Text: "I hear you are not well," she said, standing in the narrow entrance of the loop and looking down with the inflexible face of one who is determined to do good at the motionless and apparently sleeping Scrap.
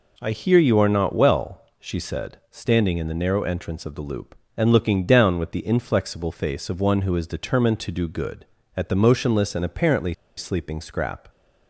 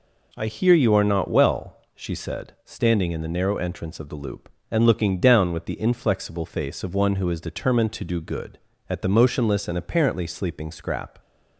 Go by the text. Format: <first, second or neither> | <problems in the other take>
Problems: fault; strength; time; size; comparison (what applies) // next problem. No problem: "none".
second | pauses between "apparently" and "sleeping"; slight; at 10.1 s; 0.22 s long